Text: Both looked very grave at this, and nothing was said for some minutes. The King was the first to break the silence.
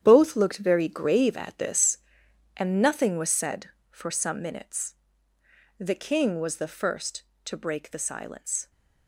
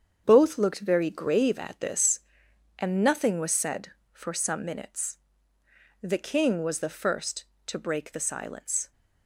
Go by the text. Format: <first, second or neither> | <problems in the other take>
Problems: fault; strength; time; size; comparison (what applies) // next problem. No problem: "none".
second | gets quieter; strong; throughout; 11 dB // starts louder than the rest; strong; until 1.0 s; 9.5 dB; strong in the second